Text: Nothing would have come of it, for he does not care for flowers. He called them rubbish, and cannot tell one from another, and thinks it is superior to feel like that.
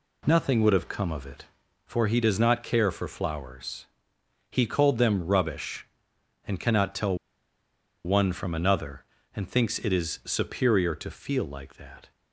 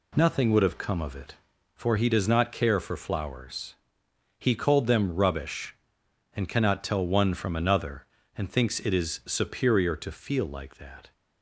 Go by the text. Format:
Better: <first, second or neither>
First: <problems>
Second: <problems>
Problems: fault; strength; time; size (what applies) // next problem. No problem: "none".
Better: second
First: pauses between "tell" and "one"; noticeable; at 7.1 s; 0.88 s long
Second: none